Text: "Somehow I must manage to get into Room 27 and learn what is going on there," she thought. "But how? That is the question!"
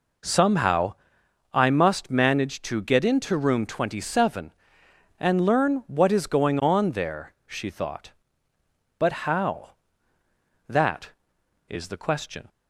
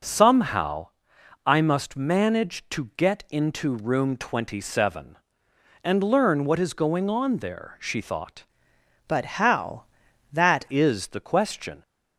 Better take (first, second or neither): first